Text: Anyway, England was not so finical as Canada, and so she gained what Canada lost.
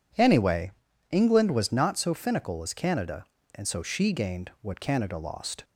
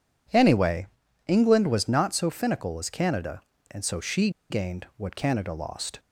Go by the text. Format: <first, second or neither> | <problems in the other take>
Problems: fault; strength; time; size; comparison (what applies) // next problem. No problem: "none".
first | pauses between "she" and "gained"; slight; at 4.2 s; 0.20 s long